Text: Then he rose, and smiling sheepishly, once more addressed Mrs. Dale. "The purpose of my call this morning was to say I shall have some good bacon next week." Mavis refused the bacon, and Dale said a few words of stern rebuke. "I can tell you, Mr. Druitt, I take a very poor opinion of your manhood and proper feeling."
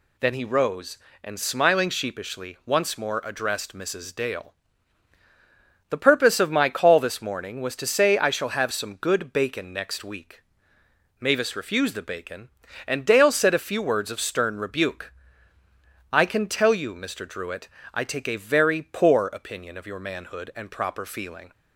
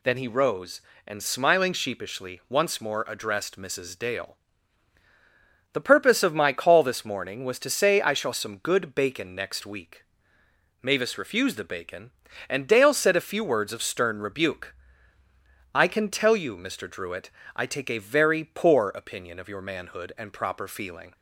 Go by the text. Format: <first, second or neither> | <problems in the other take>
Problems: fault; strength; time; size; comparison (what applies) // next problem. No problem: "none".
first | skips "have"; at 8.3 s